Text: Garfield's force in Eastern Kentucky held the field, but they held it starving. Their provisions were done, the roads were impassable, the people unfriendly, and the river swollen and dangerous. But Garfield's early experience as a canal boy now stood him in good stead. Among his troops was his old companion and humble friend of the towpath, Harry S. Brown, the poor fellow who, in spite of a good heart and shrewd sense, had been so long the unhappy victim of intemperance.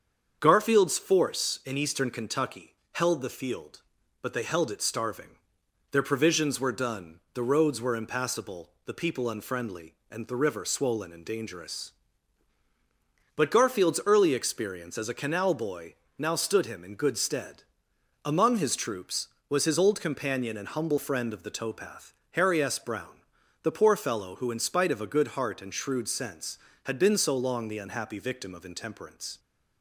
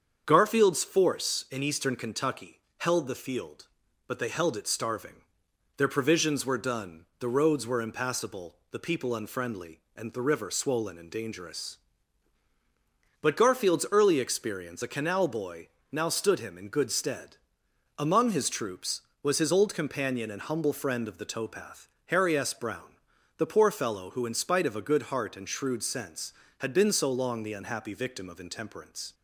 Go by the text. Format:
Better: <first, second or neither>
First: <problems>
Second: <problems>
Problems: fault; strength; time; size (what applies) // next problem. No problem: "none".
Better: first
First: starts louder than the rest; until 1.4 s; 7 dB // pauses between "Kentucky" and "held"; slight; at 2.7 s; 0.20 s long // pauses between "boy" and "now"; slight; at 15.9 s; 0.22 s long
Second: starts louder than the rest; until 1.2 s; 7 dB // pauses between "Kentucky" and "held"; slight; at 2.5 s; 0.20 s long // skips "as"; at 14.8 s // pauses between "boy" and "now"; slight; at 15.6 s; 0.22 s long